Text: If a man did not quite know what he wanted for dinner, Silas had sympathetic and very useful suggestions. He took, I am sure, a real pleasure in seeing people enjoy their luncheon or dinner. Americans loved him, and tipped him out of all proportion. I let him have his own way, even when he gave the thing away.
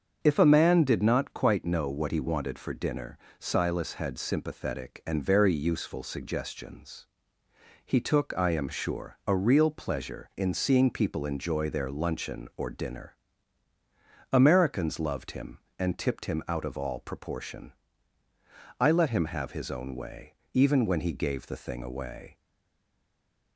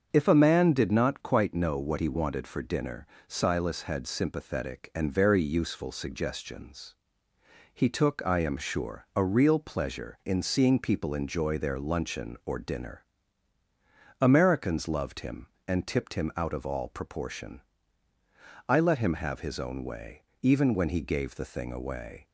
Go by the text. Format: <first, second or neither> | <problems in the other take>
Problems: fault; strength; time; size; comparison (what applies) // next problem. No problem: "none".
second | starts louder than the rest; until 1.2 s; 7 dB; also in the second // stays silent after the last word; noticeable; from 22.3 s on; 1.2 s long